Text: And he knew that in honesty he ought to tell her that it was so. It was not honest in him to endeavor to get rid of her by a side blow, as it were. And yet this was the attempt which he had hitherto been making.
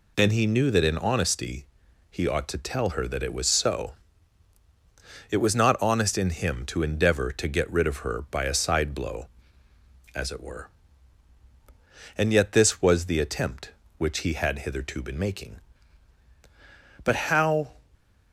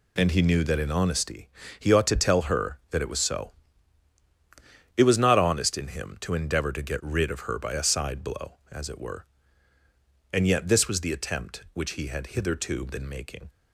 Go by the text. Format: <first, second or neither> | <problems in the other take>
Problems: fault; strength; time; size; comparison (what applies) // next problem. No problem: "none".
second | pauses between "honesty" and "he"; noticeable; at 1.6 s; 0.46 s long; slight in the second // goes on to say "But how"; noticeable; from 17.0 s on; 0.68 s long